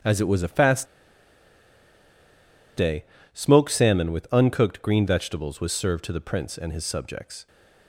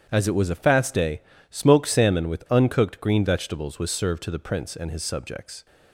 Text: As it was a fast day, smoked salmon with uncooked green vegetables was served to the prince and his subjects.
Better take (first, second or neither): second